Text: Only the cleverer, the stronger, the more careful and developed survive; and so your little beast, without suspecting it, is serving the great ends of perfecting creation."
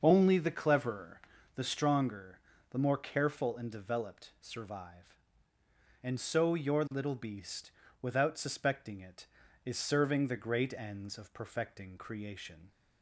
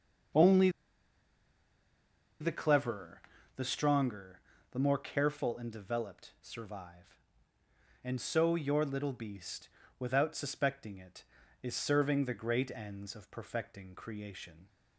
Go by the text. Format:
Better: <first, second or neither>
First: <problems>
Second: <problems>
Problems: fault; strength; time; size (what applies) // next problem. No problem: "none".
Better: first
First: starts louder than the rest; until 1.0 s; 6.5 dB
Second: starts louder than the rest; until 3.0 s; 6.5 dB // pauses between "Only" and "the"; strong; at 0.6 s; 1.7 s long